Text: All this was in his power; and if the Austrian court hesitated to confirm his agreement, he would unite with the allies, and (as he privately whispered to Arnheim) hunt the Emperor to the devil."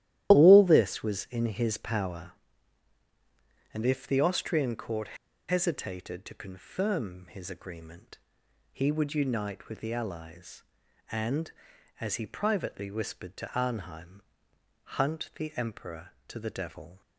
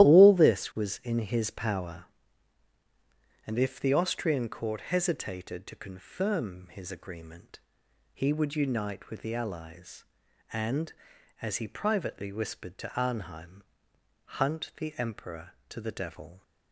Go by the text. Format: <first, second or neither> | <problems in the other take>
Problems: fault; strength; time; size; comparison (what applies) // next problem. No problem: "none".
second | starts louder than the rest; strong; until 1.3 s; 13 dB; strong in the second // pauses between "court" and "hesitated"; slight; at 5.1 s; 0.34 s long